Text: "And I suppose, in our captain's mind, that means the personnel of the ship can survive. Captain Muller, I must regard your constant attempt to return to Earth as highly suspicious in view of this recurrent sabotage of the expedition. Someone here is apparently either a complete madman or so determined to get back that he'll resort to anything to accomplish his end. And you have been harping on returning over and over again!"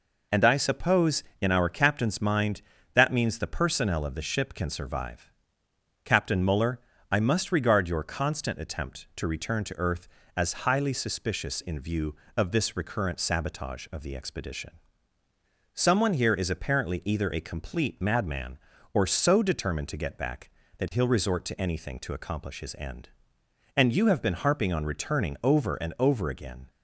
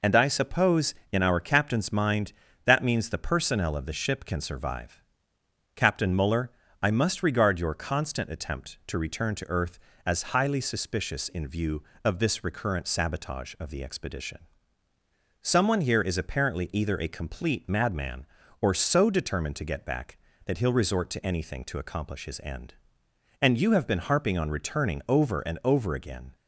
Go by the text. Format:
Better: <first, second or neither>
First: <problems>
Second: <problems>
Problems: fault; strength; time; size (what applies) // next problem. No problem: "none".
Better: neither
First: none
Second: none